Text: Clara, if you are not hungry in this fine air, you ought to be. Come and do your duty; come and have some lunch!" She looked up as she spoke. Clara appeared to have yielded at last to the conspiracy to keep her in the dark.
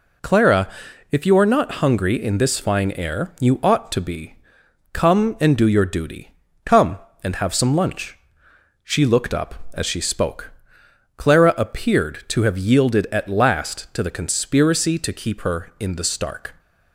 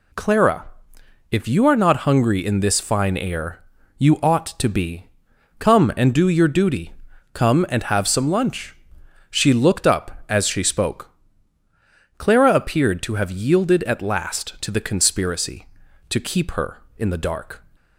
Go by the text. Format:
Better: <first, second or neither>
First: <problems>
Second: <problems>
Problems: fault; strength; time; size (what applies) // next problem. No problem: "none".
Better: second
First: says "stark" for "dark"; at 16.0 s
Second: none